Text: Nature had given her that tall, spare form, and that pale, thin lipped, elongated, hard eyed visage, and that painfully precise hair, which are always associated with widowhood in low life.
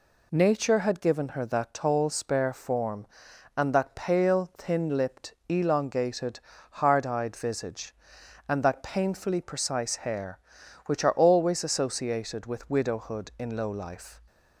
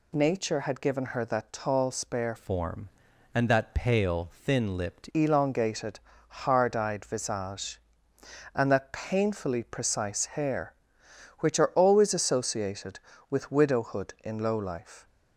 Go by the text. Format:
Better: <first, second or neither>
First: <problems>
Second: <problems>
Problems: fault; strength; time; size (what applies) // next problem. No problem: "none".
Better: first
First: none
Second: changes voice from "form" to "lipped"; from 2.3 to 5.0 s; 2.7 s long